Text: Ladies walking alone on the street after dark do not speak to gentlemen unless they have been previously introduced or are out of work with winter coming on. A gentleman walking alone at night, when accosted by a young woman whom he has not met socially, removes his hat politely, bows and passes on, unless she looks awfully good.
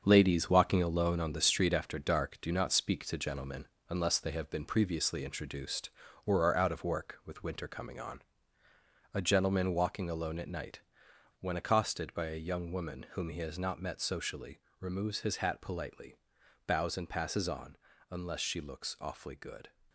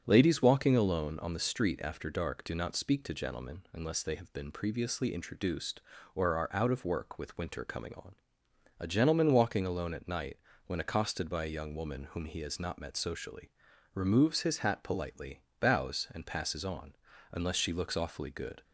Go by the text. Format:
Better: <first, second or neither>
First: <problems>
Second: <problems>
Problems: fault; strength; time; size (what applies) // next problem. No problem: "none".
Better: second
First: gets quieter; strong; throughout; 7.5 dB // starts louder than the rest; until 1.0 s; 7 dB // pauses between "gentlemen" and "unless"; slight; at 3.6 s; 0.20 s long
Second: starts louder than the rest; strong; until 1.0 s; 7.5 dB